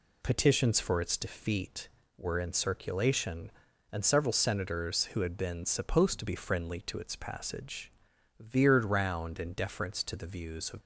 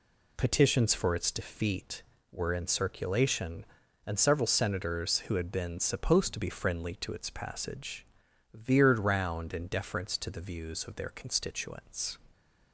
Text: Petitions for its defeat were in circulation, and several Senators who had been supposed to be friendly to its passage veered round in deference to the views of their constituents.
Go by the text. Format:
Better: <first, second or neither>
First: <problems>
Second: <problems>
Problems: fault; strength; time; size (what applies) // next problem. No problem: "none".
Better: second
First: pauses between "passage" and "veered"; noticeable; at 7.9 s; 0.48 s long // stops before "their constituents"; at 10.8 s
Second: pauses between "passage" and "veered"; noticeable; at 8.0 s; 0.48 s long